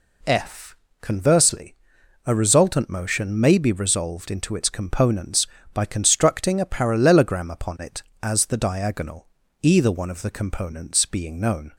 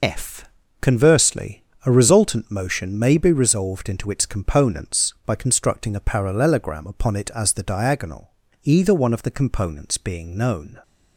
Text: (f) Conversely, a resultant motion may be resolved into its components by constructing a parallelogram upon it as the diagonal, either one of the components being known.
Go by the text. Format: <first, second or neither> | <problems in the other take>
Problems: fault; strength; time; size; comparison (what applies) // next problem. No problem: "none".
first | loses the start of "f"; at 0.0 s; 60 ms